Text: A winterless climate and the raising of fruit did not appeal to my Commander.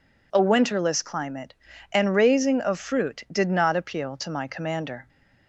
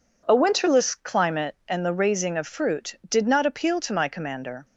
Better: second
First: skips "the"; at 2.1 s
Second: none

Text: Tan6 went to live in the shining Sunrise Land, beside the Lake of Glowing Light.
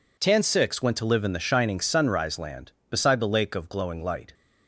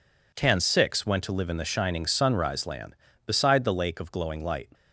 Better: neither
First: none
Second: none

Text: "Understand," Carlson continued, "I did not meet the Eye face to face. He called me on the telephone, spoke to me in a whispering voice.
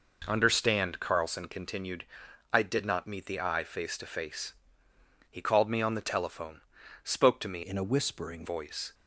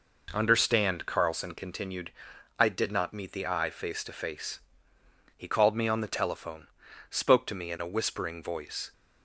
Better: second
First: changes voice from "in" to "whispering"; from 7.6 to 8.4 s; 0.8 s long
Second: none

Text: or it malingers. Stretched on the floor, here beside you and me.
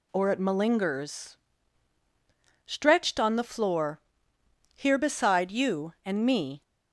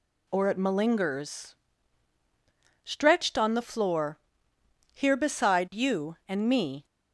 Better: neither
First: none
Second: none

